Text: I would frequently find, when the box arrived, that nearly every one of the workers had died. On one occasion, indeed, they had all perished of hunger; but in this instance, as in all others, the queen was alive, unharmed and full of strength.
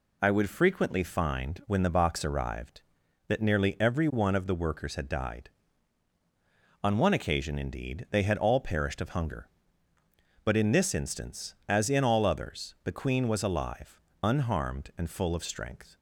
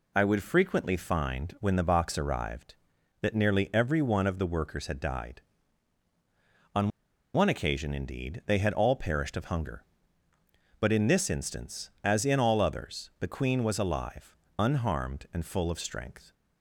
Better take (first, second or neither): first